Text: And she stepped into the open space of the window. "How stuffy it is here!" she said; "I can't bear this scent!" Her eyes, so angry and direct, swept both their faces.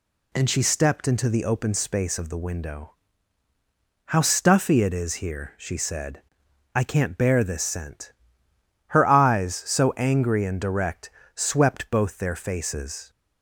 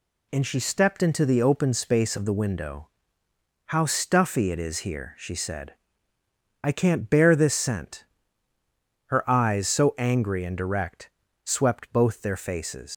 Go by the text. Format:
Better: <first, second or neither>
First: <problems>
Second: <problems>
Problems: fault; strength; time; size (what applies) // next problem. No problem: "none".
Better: first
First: none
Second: leaves "faces" unfinished; at 12.9 s; 100 ms